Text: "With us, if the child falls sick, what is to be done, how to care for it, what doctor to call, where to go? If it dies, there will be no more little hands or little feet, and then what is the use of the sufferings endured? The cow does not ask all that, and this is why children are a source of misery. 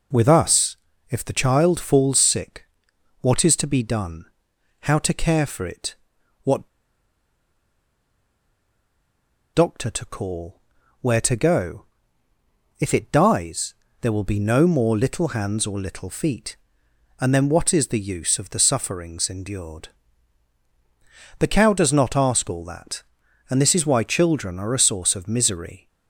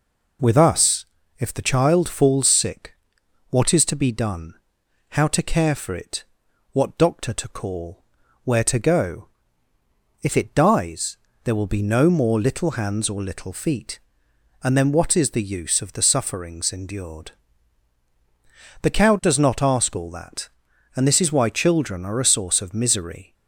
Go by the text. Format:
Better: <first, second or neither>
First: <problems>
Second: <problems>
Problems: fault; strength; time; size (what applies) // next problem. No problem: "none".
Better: second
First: pauses between "what" and "doctor"; strong; at 6.6 s; 2.8 s long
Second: none